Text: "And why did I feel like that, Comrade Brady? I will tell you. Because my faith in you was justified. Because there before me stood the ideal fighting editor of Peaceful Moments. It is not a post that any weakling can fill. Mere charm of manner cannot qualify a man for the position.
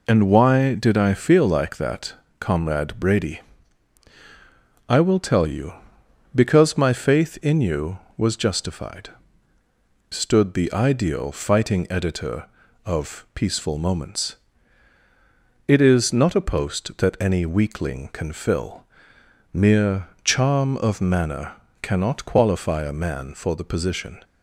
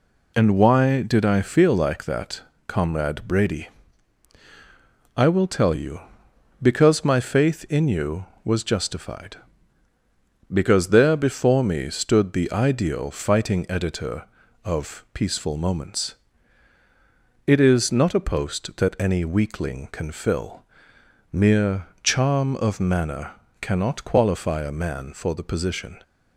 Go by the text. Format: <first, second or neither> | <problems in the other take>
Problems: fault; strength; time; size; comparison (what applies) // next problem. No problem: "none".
second | skips "Because there before me"; at 9.6 s // pauses between "Mere" and "charm"; slight; at 20.0 s; 0.16 s long; slight in the second // pauses between "manner" and "cannot"; slight; at 21.5 s; 0.30 s long; slight in the second